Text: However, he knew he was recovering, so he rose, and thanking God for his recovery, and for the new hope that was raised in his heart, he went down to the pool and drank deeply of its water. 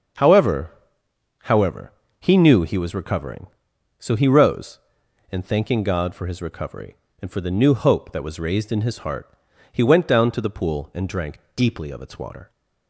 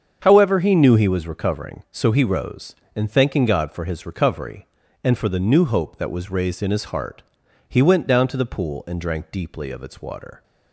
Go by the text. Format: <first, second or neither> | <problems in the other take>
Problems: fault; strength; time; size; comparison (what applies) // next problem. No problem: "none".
second | starts louder than the rest; until 1.9 s; 6.5 dB; also in the second // says "However" twice; at 1.4 s // pauses between "drank" and "deeply"; slight; at 11.4 s; 0.16 s long